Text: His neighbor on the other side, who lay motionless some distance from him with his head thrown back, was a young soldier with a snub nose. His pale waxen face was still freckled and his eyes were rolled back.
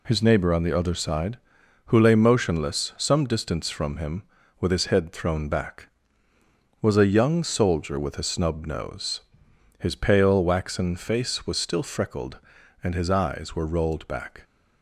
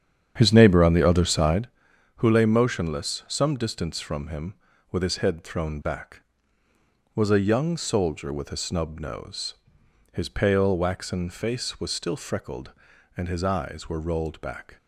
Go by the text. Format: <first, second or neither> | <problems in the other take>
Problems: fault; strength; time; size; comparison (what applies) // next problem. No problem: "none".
first | starts louder than the rest; strong; until 1.7 s; 8.5 dB